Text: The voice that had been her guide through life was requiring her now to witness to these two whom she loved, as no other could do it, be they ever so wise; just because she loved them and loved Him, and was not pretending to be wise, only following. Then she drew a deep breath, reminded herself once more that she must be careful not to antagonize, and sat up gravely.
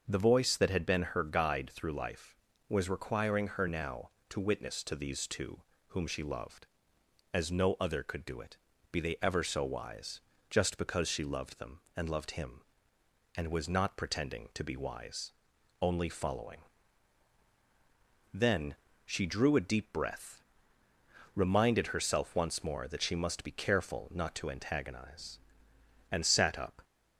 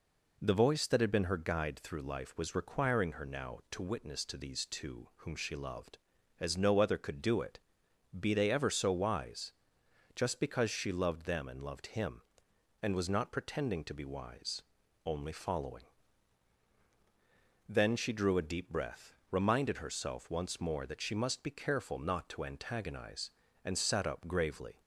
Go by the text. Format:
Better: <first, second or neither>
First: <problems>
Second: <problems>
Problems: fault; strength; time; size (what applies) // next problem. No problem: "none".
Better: second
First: starts louder than the rest; until 1.1 s; 6.5 dB // pauses between "two" and "whom"; slight; at 5.6 s; 0.26 s long // pauses between "Then" and "she"; slight; at 18.7 s; 0.30 s long // stops before "gravely"; at 26.8 s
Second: none